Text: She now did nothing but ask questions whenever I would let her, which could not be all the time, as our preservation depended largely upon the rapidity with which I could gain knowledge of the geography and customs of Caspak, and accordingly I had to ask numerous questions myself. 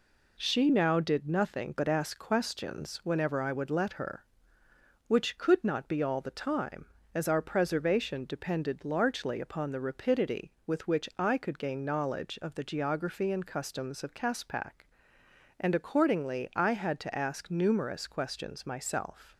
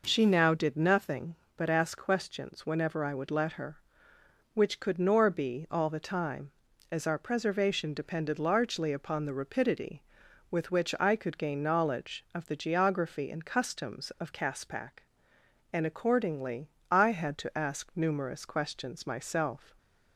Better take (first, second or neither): first